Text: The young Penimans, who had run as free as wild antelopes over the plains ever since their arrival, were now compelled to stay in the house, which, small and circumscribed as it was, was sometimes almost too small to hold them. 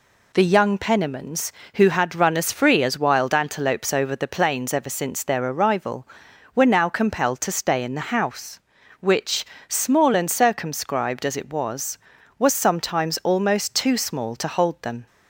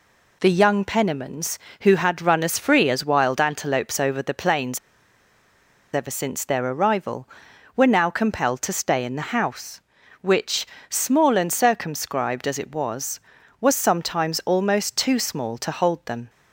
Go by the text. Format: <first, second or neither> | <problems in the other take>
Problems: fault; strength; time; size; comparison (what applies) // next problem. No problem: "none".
first | pauses between "plains" and "ever"; at 4.7 s; 1.1 s long